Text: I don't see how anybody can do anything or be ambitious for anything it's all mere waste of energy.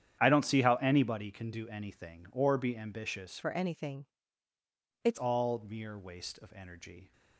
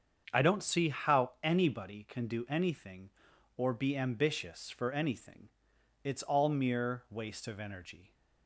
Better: second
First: starts louder than the rest; strong; until 1.2 s; 9.5 dB // changes voice from "for" to "it's"; from 3.4 to 5.1 s; 1.7 s long // pauses between "anything" and "it's"; noticeable; at 4.0 s; 0.96 s long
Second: starts louder than the rest; strong; until 1.4 s; 7 dB // pauses between "anything" and "it's"; noticeable; at 5.4 s; 0.56 s long

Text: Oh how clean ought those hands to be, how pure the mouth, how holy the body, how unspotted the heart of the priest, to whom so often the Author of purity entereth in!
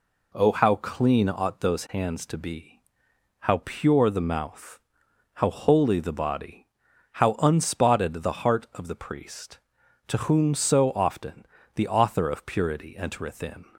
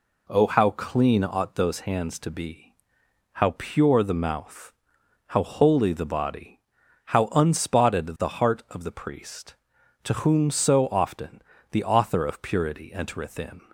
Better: neither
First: pauses between "often" and "the"; slight; at 11.4 s; 0.30 s long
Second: pauses between "often" and "the"; slight; at 11.4 s; 0.30 s long

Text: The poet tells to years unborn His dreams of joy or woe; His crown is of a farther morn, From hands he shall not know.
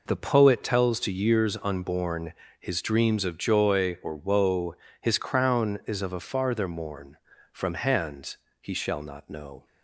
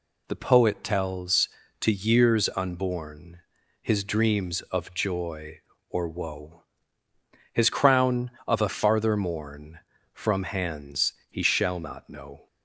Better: first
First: pauses between "unborn" and "His"; slight; at 2.3 s; 0.28 s long // pauses between "hands" and "he"; slight; at 8.3 s; 0.24 s long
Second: pauses between "unborn" and "His"; at 3.4 s; 0.42 s long // skips "is"; at 8.3 s // pauses between "hands" and "he"; slight; at 11.1 s; 0.16 s long

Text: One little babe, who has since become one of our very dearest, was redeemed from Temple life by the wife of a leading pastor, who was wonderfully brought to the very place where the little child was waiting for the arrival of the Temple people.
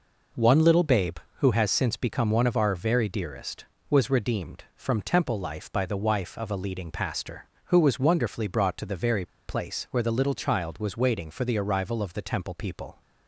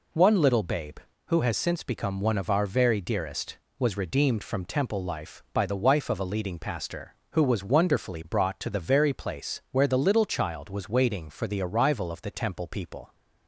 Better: second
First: pauses between "very" and "place"; slight; at 9.2 s; 0.20 s long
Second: none

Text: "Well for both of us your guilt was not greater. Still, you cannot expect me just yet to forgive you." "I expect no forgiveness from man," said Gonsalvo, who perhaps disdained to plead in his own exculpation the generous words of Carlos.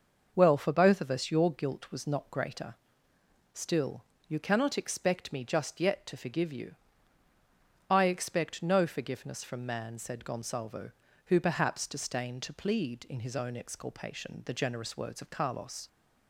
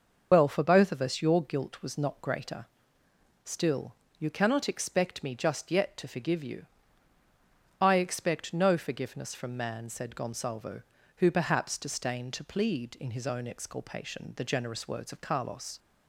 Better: first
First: starts louder than the rest; noticeable; until 1.3 s; 6 dB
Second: loses the start of "Well"; at 0.3 s; 55 ms // starts louder than the rest; noticeable; until 1.3 s; 6 dB

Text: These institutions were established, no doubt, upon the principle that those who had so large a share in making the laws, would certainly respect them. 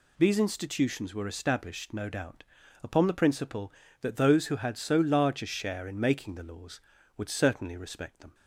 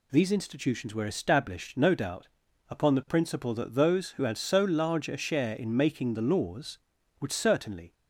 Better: first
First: none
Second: stops before "respect them"; at 7.9 s

